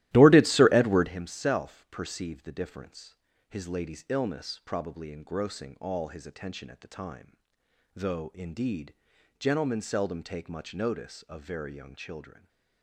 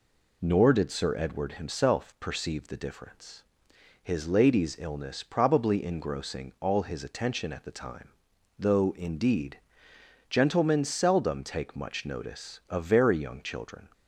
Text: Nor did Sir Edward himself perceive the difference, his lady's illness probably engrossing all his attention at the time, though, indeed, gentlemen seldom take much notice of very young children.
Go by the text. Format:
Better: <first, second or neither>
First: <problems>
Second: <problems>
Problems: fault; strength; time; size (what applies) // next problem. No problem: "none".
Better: second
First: starts louder than the rest; strong; until 1.2 s; 15 dB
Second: none